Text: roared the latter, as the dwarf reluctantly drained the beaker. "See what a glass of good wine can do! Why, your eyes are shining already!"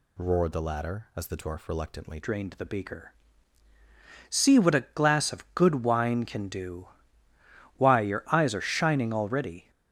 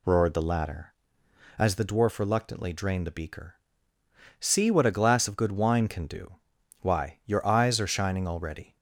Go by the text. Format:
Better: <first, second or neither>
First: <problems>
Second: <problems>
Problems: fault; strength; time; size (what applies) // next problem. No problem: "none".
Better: second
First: changes voice at "drained"; from 2.2 s on; 7.5 s long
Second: none